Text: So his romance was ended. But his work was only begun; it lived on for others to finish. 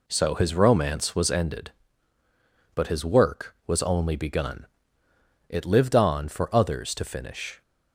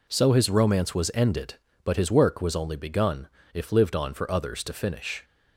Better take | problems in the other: first | says "if" for "it"; at 3.5 s

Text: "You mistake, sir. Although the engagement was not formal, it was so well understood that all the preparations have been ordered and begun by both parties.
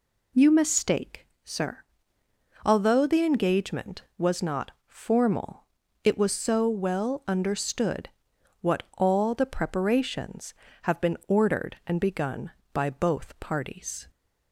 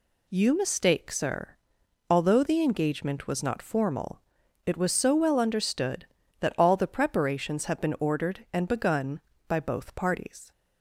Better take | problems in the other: second | pauses between "not" and "formal"; slight; at 4.7 s; 0.16 s long // says "what" for "that"; at 8.6 s

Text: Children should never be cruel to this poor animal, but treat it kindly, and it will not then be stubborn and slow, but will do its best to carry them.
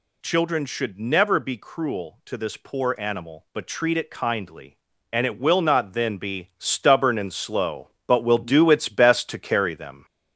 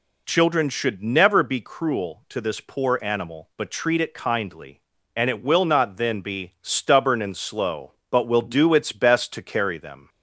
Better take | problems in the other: second | gets louder; slight; throughout; 3 dB

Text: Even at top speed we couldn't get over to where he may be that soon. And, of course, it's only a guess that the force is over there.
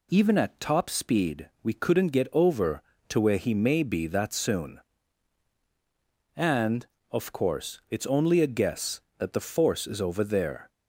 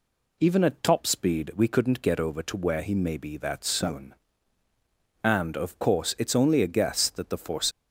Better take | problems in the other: first | stops before "is over there"; at 7.7 s

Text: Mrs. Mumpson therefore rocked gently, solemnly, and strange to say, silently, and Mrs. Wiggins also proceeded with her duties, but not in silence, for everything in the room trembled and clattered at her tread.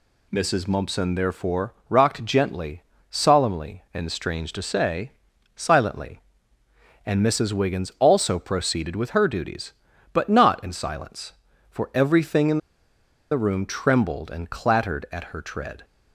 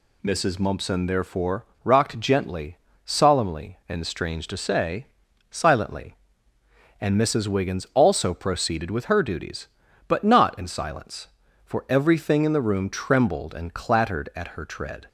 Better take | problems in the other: second | pauses between "therefore" and "rocked"; slight; at 1.7 s; 0.16 s long; slight in the second // pauses between "in" and "the"; noticeable; at 12.5 s; 0.73 s long

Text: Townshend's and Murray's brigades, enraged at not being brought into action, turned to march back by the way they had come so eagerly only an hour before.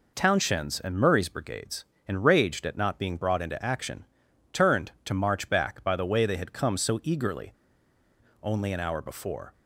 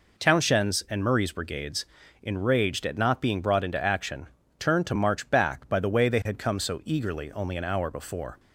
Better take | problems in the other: second | pauses between "eagerly" and "only"; noticeable; at 7.5 s; 0.88 s long

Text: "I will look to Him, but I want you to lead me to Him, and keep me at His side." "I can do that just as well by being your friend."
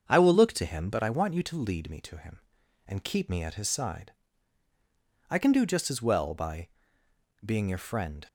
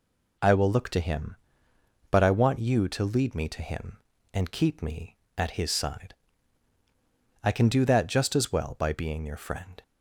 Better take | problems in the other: second | starts louder than the rest; until 1.1 s; 6.5 dB // skips "that"; at 5.6 s // pauses between "by" and "being"; noticeable; at 6.6 s; 0.76 s long

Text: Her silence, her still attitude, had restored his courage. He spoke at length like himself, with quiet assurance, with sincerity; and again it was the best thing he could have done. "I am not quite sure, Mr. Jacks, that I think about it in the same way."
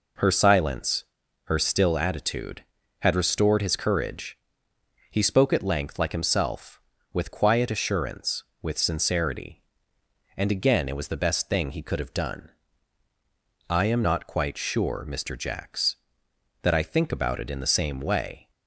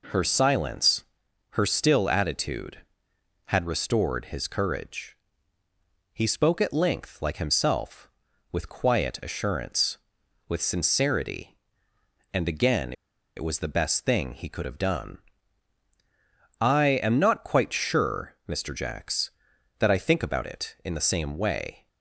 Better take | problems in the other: first | pauses between "again" and "it"; at 12.9 s; 0.44 s long

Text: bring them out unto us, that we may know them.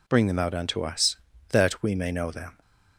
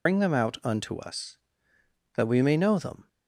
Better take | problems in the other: first | loses the start of "bring"; at 0.0 s; 75 ms

